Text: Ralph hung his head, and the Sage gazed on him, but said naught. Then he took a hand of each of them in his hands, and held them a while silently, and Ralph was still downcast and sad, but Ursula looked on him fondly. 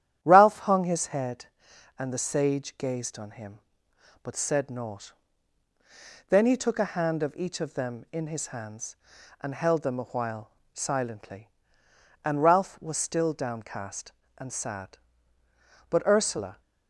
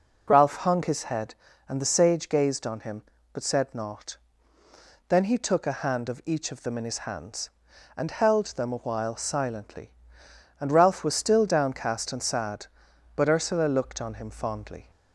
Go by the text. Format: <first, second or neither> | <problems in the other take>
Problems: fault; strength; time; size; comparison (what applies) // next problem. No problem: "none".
second | starts louder than the rest; strong; until 1.2 s; 10.5 dB // pauses between "while" and "silently"; slight; at 10.5 s; 0.24 s long // stops before "looked on him fondly"; at 16.6 s